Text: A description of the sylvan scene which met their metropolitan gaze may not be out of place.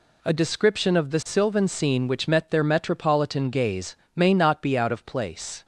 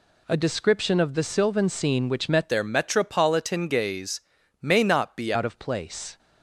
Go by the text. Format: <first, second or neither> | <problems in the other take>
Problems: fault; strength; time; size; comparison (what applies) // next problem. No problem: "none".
first | changes voice from "their" to "be"; from 2.5 to 5.3 s; 2.8 s long // pauses between "gaze" and "may"; at 4.2 s; 0.42 s long; slight in the first